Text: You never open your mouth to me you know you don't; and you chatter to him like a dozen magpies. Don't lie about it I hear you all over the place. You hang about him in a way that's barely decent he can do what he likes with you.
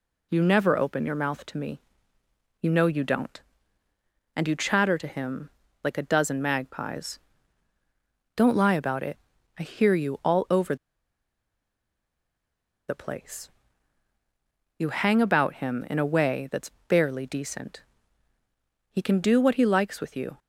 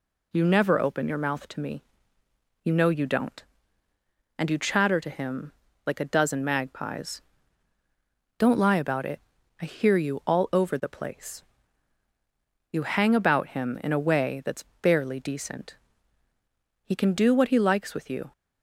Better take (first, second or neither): second